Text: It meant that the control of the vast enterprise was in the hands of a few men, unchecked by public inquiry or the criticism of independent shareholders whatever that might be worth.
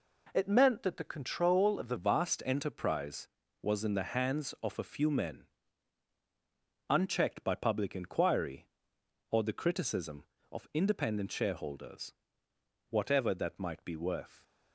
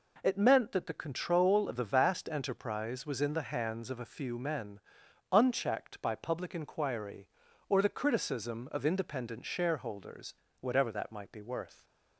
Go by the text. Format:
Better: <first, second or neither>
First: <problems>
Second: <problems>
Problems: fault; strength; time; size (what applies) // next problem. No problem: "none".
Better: second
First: changes voice at "vast"; from 1.9 s on; 12.5 s long // pauses between "shareholders" and "whatever"; noticeable; at 12.1 s; 0.76 s long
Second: pauses between "shareholders" and "whatever"; slight; at 10.3 s; 0.26 s long